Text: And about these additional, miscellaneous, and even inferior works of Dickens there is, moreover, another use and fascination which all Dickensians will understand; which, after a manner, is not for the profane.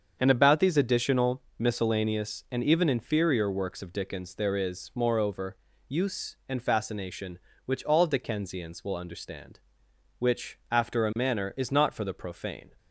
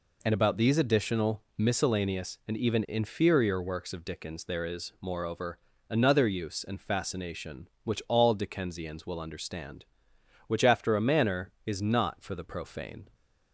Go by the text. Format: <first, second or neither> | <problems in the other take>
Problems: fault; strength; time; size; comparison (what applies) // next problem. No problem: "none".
second | starts louder than the rest; strong; until 1.2 s; 7 dB // skips "another"; at 5.7 s